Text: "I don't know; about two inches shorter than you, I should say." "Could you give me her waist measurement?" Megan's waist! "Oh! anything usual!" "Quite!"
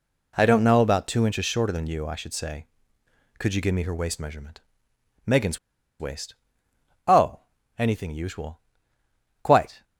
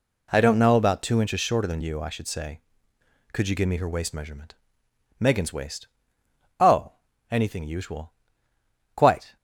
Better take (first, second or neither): second